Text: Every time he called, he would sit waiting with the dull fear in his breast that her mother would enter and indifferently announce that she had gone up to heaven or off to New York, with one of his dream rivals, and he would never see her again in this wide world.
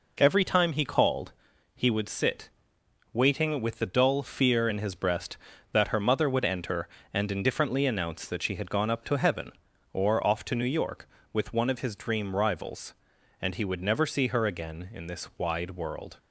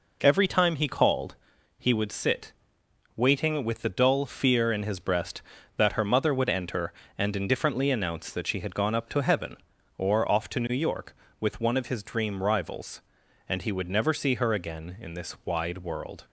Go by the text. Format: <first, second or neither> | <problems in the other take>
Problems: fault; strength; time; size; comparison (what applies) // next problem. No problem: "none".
neither | pauses between "sit" and "waiting"; noticeable; the same in both